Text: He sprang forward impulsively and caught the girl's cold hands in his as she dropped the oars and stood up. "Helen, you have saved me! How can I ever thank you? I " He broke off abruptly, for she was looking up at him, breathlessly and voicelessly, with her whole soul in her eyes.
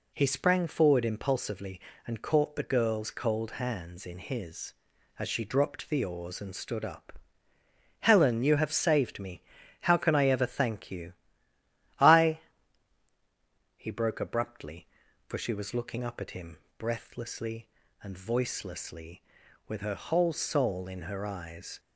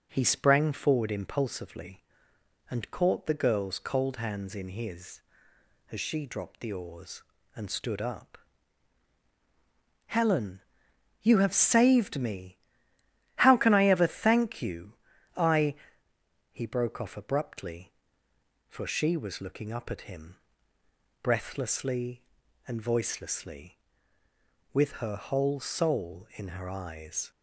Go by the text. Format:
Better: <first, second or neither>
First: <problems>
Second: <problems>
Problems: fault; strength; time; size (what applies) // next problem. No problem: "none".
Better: second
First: skips "off"; at 14.1 s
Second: none